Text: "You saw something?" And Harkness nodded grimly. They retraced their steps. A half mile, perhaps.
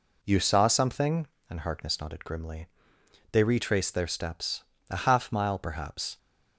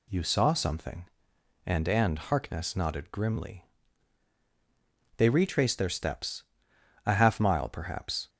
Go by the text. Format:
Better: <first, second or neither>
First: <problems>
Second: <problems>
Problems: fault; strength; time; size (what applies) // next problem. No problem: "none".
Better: first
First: none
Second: says "And" twice; at 1.8 s